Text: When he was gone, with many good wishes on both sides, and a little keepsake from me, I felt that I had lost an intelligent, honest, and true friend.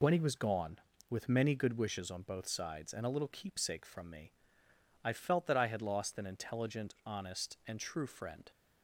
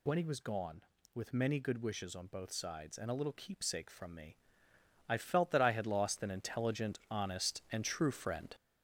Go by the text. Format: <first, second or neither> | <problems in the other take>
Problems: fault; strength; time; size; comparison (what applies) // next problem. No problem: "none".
first | gets louder; noticeable; throughout; 5.5 dB